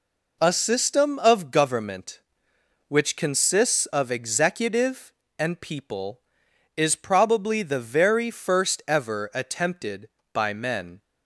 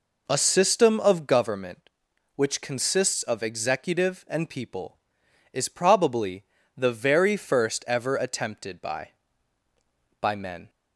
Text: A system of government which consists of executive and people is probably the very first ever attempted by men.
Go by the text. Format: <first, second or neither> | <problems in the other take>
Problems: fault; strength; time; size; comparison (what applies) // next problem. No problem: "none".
first | pauses between "probably" and "the"; slight; at 6.4 s; 0.32 s long // says "by" twice; at 10.1 s